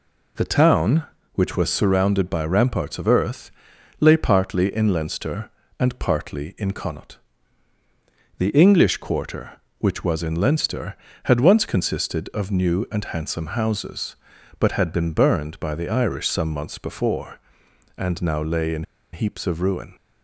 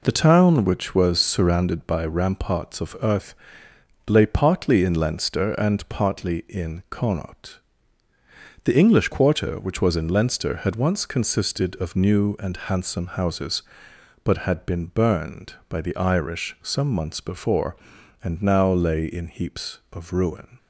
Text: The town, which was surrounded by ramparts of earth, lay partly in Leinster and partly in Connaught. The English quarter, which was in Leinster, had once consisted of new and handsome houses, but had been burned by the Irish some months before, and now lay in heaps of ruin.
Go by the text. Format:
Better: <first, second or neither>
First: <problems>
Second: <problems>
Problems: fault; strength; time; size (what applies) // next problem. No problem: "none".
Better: second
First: pauses between "in" and "heaps"; slight; at 18.8 s; 0.30 s long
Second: none